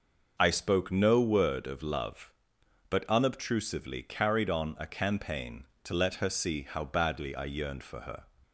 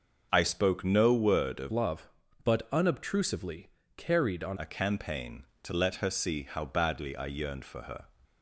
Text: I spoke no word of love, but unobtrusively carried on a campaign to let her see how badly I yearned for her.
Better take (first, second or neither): first